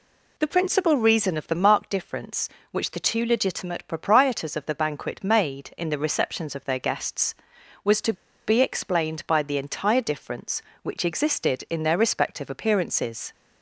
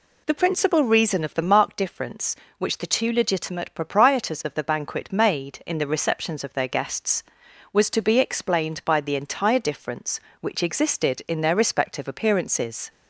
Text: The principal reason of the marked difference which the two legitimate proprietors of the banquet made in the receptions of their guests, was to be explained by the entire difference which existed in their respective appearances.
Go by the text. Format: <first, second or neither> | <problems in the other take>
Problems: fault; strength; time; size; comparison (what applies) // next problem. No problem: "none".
second | pauses between "to" and "be"; slight; at 8.1 s; 0.33 s long